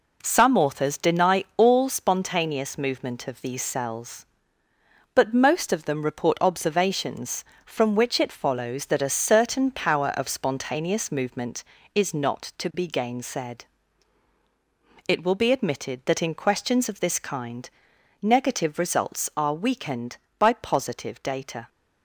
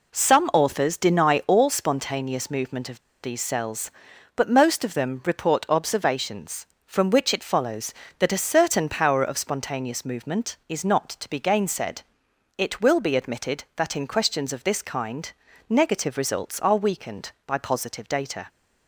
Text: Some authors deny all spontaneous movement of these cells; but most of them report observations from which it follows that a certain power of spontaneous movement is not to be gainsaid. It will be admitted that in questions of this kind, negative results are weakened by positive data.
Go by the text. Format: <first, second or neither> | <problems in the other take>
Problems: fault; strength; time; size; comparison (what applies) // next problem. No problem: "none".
first | pauses between "of" and "these"; slight; at 2.9 s; 0.22 s long